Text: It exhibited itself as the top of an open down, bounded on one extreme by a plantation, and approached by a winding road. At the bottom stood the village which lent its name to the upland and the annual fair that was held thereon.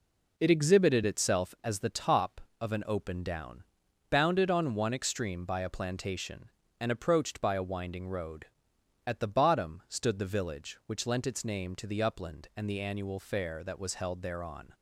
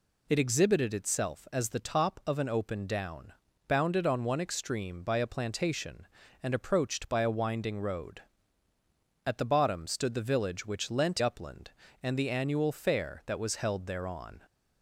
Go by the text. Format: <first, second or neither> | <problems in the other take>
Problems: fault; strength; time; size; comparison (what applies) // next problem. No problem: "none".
first | skips "its name to the"; at 11.2 s